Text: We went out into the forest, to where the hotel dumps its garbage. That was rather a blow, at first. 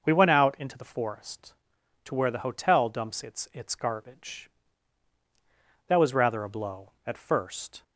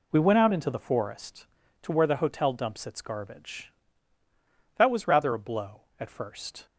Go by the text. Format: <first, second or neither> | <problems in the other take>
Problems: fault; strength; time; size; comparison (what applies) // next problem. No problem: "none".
second | says "its" twice; at 3.5 s